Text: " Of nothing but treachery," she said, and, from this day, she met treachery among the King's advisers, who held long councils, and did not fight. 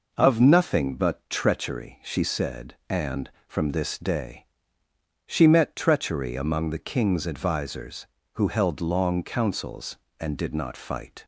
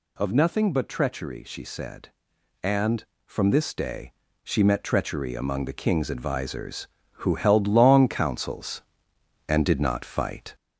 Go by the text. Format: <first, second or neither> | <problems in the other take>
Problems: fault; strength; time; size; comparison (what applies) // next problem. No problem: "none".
first | gets louder; throughout; 3.5 dB